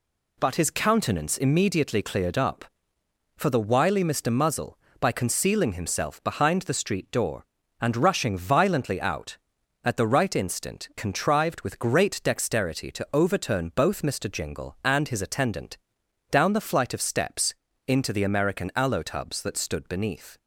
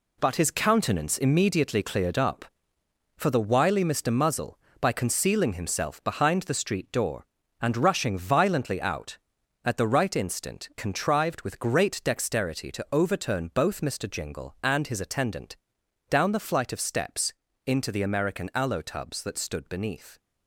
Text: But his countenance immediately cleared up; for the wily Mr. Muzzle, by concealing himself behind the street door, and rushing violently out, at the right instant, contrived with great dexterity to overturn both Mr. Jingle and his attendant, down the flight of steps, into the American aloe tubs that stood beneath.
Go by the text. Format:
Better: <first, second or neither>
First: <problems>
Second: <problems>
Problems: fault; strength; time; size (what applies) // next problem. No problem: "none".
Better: first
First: none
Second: gets quieter; strong; throughout; 8 dB